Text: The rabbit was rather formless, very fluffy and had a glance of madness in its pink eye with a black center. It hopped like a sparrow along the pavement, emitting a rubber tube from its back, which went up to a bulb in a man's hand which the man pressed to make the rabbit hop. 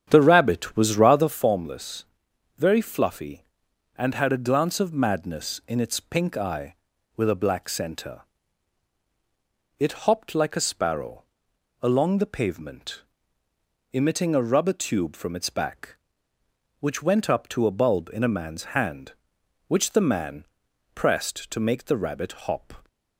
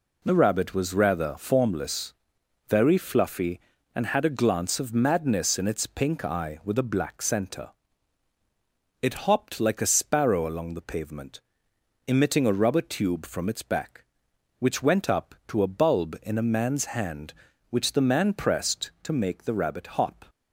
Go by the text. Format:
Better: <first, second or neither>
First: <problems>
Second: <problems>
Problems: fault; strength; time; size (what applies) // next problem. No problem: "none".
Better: second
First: starts louder than the rest; strong; until 1.4 s; 8.5 dB // pauses between "sparrow" and "along"; noticeable; at 11.2 s; 0.58 s long // pauses between "man" and "pressed"; noticeable; at 20.4 s; 0.50 s long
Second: none